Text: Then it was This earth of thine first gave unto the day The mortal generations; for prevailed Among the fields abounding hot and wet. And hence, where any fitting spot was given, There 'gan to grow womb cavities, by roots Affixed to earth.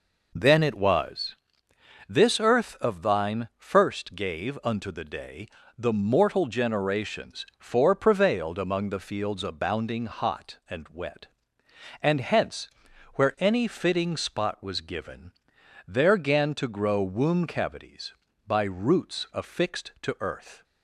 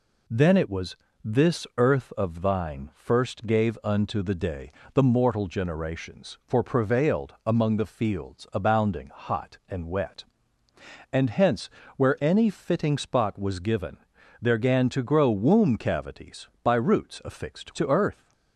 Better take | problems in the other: second | starts louder than the rest; noticeable; until 1.9 s; 4.5 dB // pauses between "was" and "This"; noticeable; at 1.3 s; 0.74 s long; slight in the second // pauses between "day" and "The"; slight; at 5.4 s; 0.30 s long; slight in the second

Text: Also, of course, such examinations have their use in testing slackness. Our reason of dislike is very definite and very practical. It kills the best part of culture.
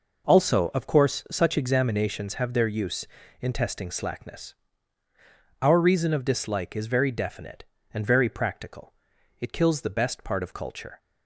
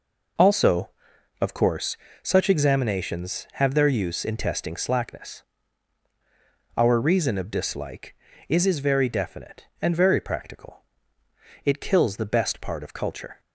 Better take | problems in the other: first | says "is" twice; at 8.6 s

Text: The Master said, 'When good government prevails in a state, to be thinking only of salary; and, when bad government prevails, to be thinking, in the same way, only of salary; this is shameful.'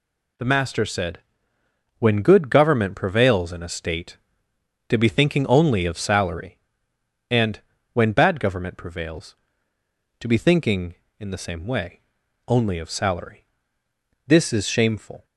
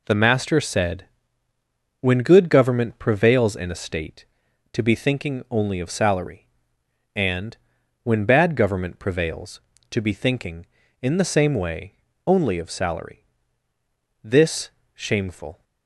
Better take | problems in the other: first | skips "is"; at 14.8 s

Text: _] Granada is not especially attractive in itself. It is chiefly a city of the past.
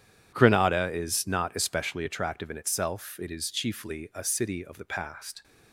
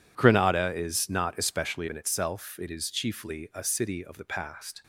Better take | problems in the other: first | skips "attractive"; at 1.8 s

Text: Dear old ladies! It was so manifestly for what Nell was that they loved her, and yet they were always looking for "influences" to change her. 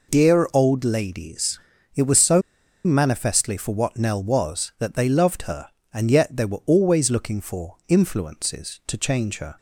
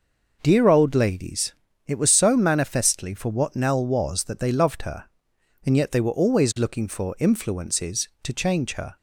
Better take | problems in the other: second | pauses between "so" and "manifestly"; at 2.4 s; 0.43 s long

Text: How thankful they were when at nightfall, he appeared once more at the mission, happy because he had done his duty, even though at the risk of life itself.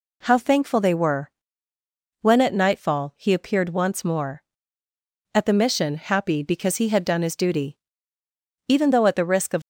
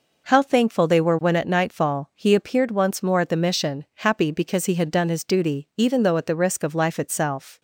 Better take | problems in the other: second | pauses between "were" and "when"; noticeable; at 1.2 s; 0.92 s long // stops before "life itself"; at 9.6 s

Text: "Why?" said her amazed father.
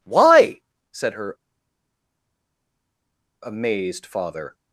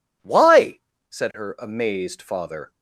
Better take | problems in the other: second | pauses between "her" and "amazed"; strong; at 1.3 s; 2.0 s long

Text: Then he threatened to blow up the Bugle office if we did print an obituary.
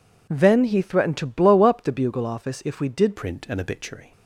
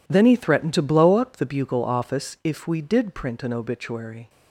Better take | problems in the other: second | changes voice at "print"; from 3.1 s on; 1.0 s long

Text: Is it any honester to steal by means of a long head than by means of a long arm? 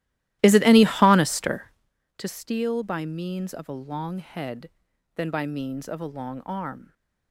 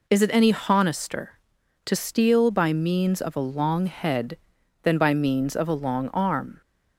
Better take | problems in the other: second | starts louder than the rest; strong; until 2.0 s; 15 dB

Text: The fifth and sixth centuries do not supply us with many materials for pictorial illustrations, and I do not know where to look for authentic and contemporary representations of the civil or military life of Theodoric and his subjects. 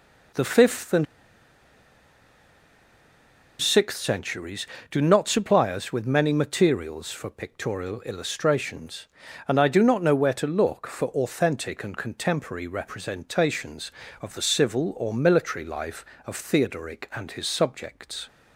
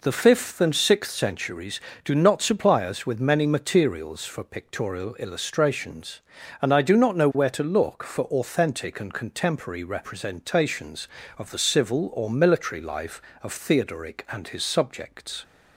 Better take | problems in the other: second | pauses between "and" and "sixth"; strong; at 1.0 s; 2.5 s long

